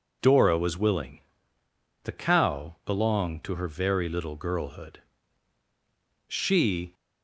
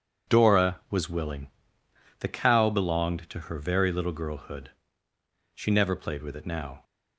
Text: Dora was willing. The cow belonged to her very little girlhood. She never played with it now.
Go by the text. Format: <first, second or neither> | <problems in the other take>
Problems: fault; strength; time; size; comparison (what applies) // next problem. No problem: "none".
second | stops before "never played with it now"; at 6.9 s